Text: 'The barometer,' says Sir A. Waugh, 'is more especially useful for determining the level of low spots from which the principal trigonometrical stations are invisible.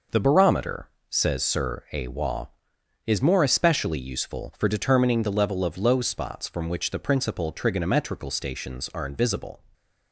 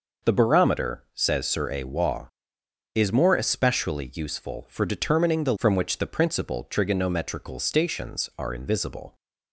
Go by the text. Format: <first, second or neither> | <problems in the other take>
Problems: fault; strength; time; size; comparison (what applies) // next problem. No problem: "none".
first | skips "level of low spots"; at 5.5 s